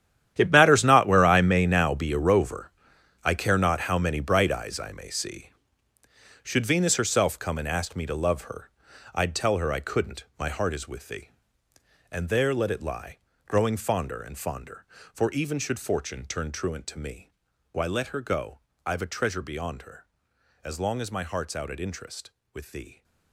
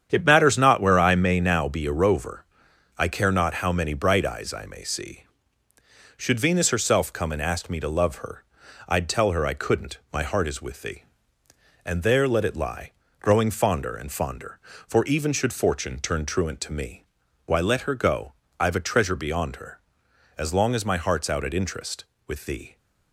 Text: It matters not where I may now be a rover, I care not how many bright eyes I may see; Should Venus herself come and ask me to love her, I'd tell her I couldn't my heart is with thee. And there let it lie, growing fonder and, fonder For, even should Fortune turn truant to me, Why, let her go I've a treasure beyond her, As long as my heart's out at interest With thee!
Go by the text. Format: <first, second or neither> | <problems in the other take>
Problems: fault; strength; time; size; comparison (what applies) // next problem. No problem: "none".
second | gets quieter; strong; throughout; 14.5 dB // starts louder than the rest; strong; until 1.3 s; 10.5 dB; strong in the second // pauses between "couldn't" and "my"; slight; at 10.2 s; 0.16 s long; slight in the second // pauses between "go" and "I've"; slight; at 18.5 s; 0.30 s long; slight in the second